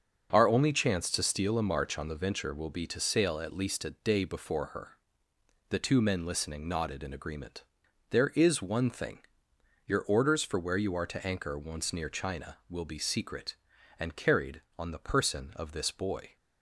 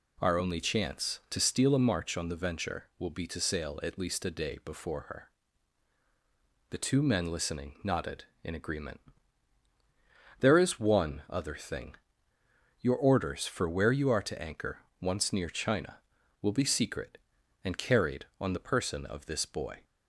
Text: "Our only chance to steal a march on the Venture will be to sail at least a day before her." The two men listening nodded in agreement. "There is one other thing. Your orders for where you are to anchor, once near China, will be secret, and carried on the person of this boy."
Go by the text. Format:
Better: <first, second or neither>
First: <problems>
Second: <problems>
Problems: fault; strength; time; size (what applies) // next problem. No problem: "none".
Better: second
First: starts louder than the rest; strong; until 1.3 s; 7.5 dB // skips "other"; at 8.8 s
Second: none